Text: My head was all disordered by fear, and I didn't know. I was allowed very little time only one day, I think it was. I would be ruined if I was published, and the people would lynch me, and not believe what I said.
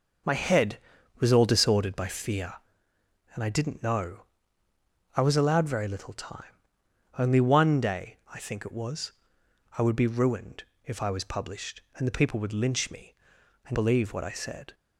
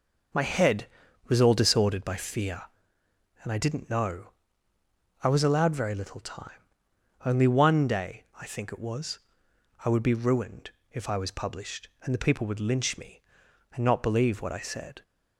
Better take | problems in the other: second | pauses between "time" and "only"; noticeable; at 6.4 s; 0.70 s long; noticeable in the second // pauses between "ruined" and "if"; slight; at 10.6 s; 0.22 s long; slight in the second // skips "not"; at 13.7 s

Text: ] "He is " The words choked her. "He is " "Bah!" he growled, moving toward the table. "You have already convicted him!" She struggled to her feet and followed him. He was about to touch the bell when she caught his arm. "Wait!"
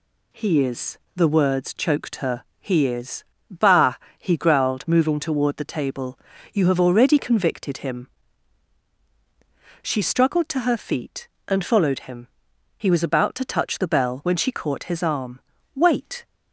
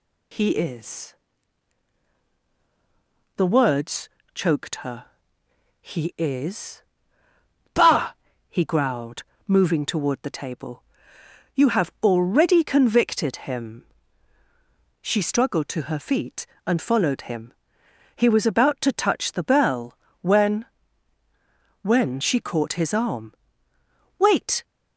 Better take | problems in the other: first | pauses between "words" and "choked"; slight; at 4.0 s; 0.24 s long // pauses between "bell" and "when"; slight; at 19.9 s; 0.24 s long // says "when" twice; at 21.8 s

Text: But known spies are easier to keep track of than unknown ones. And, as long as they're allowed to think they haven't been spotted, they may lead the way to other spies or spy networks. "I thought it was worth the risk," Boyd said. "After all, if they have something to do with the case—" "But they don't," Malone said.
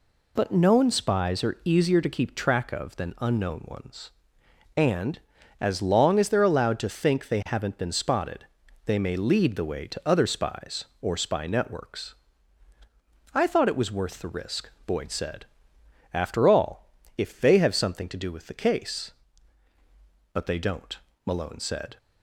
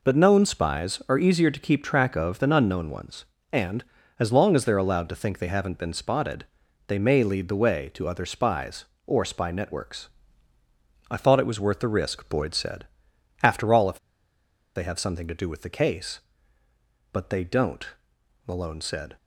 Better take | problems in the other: first | pauses between "if" and "they"; noticeable; at 13.9 s; 0.78 s long

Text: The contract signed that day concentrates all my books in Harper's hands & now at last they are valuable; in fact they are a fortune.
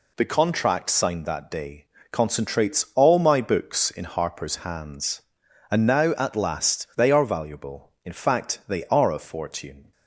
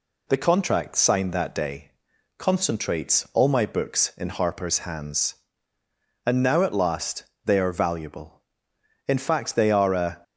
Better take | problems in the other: first | pauses between "day" and "concentrates"; noticeable; at 1.9 s; 0.46 s long; slight in the first // pauses between "last" and "they"; slight; at 7.2 s; 0.22 s long // stops before "fortune"; at 10.2 s

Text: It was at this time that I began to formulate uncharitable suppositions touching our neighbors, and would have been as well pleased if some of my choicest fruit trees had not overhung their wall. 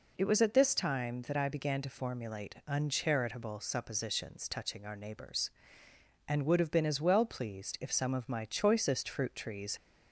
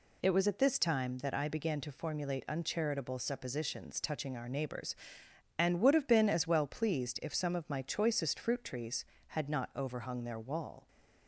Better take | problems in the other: second | stops before "had not overhung their wall"; at 9.7 s

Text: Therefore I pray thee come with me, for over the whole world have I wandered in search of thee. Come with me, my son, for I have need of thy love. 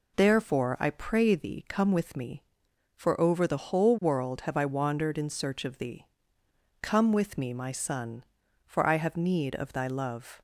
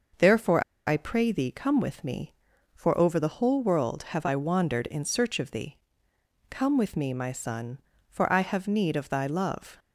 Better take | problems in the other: first | pauses between "Therefore" and "I"; slight; at 0.6 s; 0.24 s long

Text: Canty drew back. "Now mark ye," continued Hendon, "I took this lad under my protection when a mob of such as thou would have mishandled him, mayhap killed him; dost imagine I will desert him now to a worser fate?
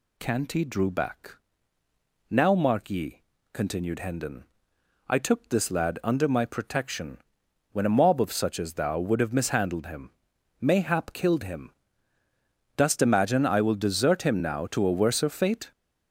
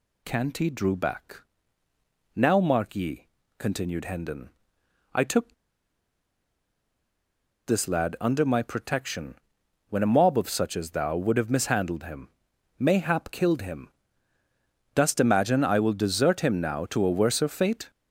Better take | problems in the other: first | pauses between "took" and "this"; strong; at 5.5 s; 2.1 s long // pauses between "protection" and "when"; noticeable; at 9.3 s; 0.56 s long; noticeable in the first

